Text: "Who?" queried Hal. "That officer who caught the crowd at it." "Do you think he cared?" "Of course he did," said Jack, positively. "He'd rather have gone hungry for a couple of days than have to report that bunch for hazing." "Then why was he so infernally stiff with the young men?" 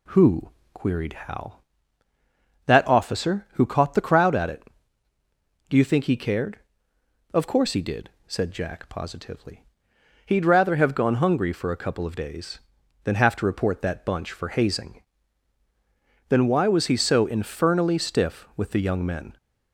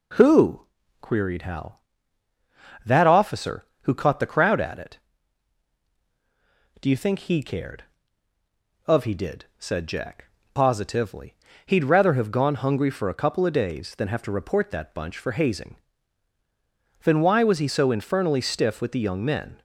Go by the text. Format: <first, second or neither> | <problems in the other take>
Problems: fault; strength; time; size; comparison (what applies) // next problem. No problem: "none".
first | skips "course"; at 9.0 s